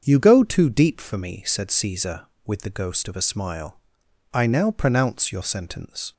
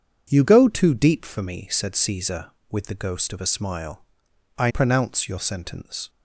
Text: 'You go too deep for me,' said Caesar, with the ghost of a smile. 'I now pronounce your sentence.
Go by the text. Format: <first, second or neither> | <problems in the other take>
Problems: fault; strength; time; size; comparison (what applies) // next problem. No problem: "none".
first | starts louder than the rest; strong; until 1.3 s; 7.5 dB; also in the first // skips "now"; at 4.7 s